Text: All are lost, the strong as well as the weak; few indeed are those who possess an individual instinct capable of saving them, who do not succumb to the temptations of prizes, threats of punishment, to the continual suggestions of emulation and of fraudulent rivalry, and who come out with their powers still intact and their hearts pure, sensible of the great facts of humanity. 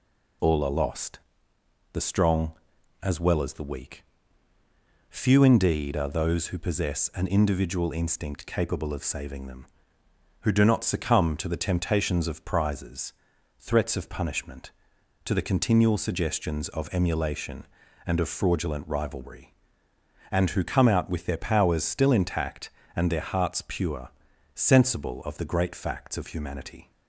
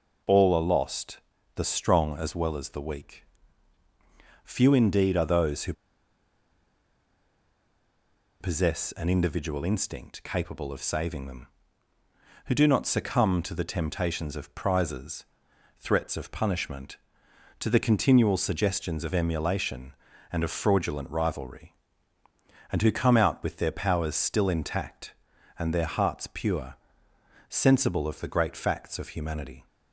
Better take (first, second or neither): first